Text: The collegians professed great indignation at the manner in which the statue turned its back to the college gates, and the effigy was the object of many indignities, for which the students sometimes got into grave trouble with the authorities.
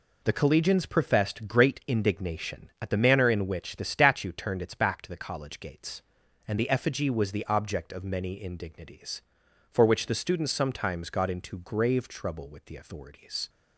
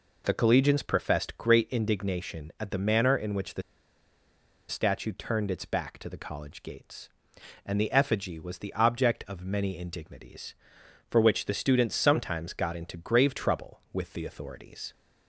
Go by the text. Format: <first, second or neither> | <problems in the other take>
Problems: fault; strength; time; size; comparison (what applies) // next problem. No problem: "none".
first | pauses between "the" and "statue"; at 3.6 s; 1.0 s long